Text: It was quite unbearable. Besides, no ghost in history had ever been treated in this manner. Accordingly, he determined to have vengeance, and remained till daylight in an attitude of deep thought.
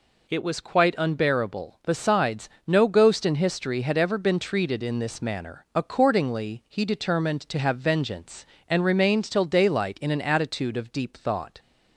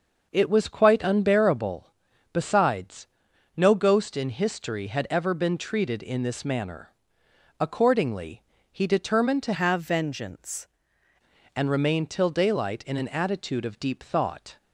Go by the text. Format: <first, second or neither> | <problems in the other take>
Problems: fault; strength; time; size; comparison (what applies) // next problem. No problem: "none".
first | changes voice from "have" to "vengeance"; from 9.5 to 10.6 s; 1.1 s long